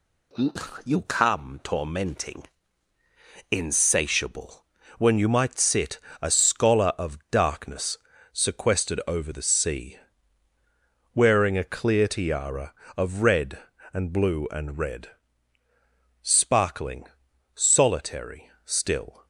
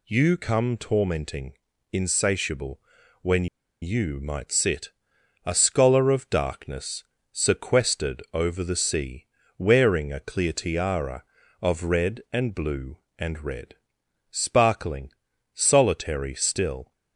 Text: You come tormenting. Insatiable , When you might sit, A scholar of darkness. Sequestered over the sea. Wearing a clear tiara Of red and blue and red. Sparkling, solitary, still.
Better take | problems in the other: first | pauses between "When" and "you"; slight; at 3.4 s; 0.35 s long

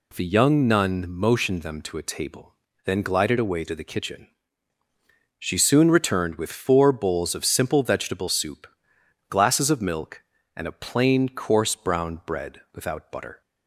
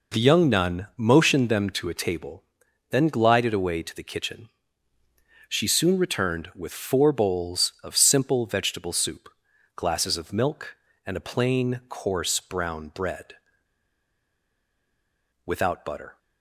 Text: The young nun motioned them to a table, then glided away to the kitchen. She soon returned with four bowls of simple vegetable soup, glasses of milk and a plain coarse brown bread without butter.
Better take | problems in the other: first | pauses between "bread" and "without"; strong; at 13.3 s; 2.1 s long

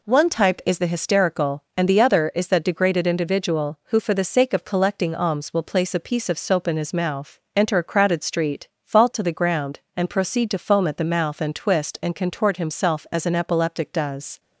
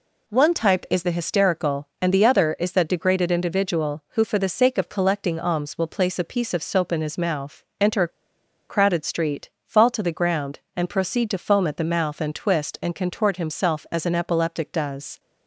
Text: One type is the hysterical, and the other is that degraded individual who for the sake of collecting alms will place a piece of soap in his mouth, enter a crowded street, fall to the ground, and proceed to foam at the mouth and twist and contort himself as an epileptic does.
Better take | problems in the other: first | pauses between "a" and "crowded"; noticeable; at 8.0 s; 0.60 s long

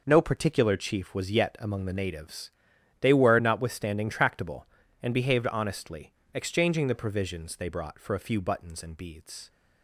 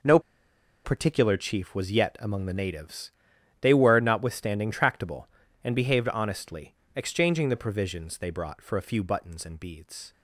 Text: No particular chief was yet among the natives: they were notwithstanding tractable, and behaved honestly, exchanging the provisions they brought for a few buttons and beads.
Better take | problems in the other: first | pauses between "No" and "particular"; noticeable; at 0.1 s; 0.65 s long

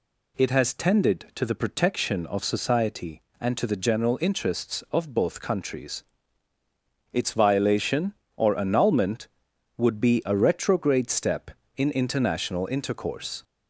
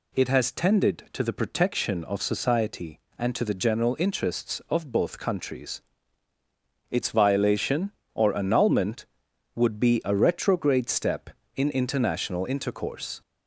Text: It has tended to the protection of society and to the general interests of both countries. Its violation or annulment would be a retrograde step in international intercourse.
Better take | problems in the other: neither | none

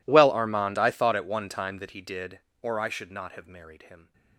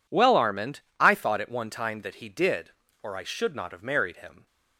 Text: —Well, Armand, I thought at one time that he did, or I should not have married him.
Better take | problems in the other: second | gets quieter; strong; throughout; 28.5 dB

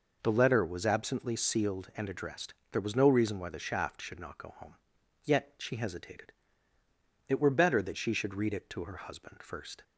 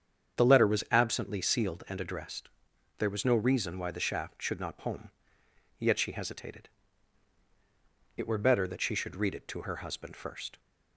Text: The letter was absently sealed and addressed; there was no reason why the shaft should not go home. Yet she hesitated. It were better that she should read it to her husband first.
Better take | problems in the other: first | starts louder than the rest; strong; until 1.4 s; 8 dB // skips "go"; at 4.7 s

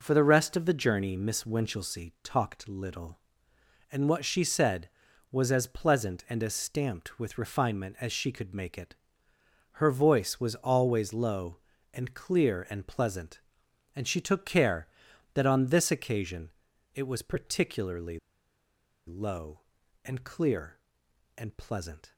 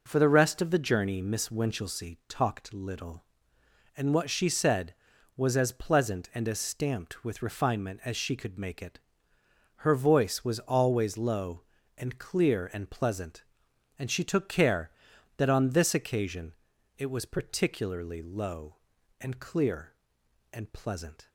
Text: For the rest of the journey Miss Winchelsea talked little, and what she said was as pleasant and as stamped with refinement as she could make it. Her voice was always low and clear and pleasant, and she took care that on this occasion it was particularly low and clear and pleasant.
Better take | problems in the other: second | pauses between "occasion" and "it"; noticeable; at 16.4 s; 0.46 s long; noticeable in the second // pauses between "particularly" and "low"; noticeable; at 18.1 s; 0.89 s long

